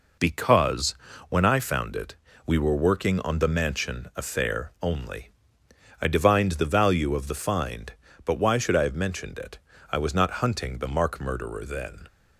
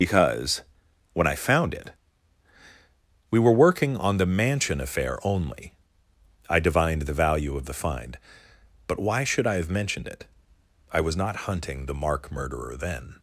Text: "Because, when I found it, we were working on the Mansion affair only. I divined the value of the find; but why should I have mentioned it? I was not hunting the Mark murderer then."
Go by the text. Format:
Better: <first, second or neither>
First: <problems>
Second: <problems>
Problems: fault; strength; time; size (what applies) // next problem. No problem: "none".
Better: first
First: none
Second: loses the start of "Because"; at 0.0 s; 65 ms